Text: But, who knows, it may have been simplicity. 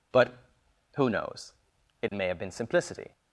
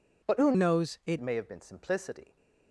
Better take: first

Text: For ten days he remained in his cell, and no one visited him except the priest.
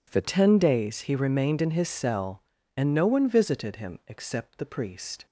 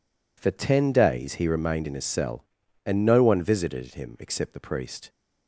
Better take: second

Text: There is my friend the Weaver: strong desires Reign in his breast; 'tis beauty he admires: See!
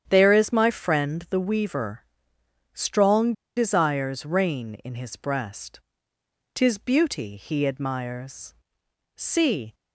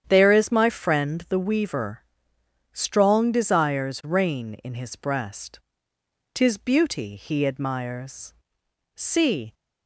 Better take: second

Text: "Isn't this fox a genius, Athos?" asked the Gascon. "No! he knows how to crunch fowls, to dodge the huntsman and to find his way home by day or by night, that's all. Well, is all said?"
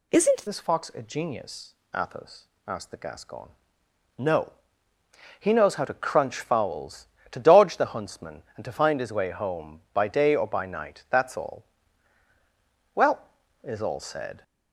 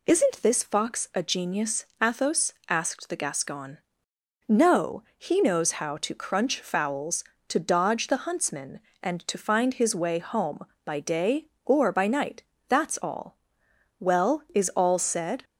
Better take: second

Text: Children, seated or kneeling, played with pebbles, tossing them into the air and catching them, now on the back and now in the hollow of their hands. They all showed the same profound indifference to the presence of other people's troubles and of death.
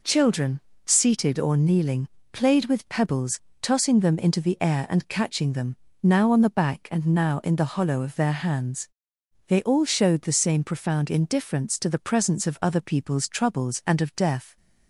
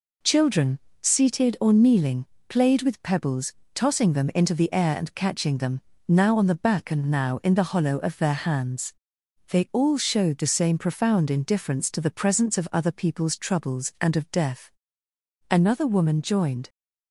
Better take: first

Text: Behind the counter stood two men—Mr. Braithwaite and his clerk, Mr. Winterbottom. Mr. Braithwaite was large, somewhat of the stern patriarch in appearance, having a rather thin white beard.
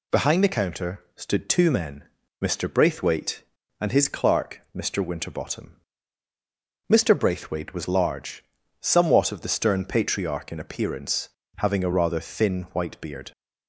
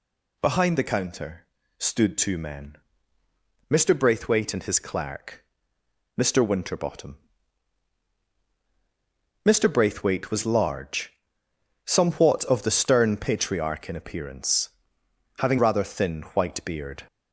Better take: first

